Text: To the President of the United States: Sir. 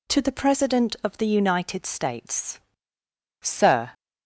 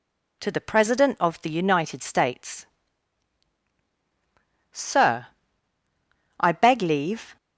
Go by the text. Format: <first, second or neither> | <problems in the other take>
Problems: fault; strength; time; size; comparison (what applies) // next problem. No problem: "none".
first | goes on to say "I beg leave"; noticeable; from 6.3 s on; 0.98 s long